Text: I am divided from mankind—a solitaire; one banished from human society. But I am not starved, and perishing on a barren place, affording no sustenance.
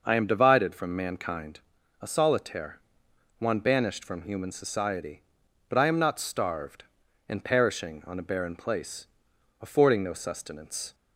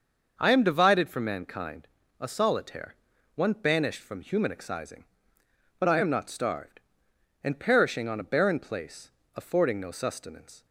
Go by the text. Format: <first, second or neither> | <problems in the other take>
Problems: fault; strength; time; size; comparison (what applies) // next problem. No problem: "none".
first | starts louder than the rest; until 1.3 s; 6 dB // says "excising" for "society"; at 4.5 s